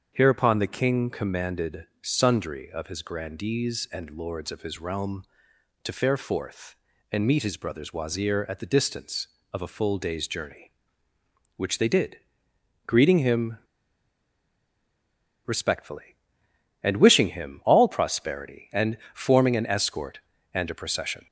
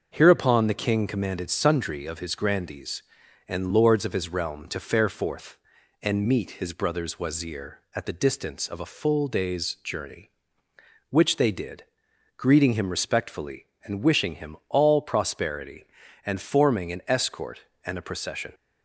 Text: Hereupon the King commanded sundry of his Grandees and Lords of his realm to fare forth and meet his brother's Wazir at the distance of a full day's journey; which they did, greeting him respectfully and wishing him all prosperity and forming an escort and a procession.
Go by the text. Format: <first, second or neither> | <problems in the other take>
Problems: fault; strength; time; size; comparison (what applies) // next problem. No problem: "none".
second | starts louder than the rest; until 1.1 s; 7 dB; also in the second // pauses between "him" and "respectfully"; strong; at 13.5 s; 1.8 s long // pauses between "and" and "forming"; slight; at 18.9 s; 0.16 s long